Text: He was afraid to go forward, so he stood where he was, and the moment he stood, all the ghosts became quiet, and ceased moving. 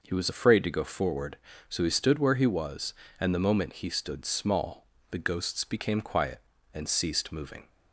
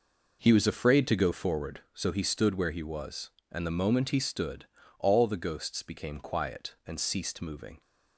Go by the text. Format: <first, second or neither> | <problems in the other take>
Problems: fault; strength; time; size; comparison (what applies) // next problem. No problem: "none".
second | says "small" for "all"; at 4.2 s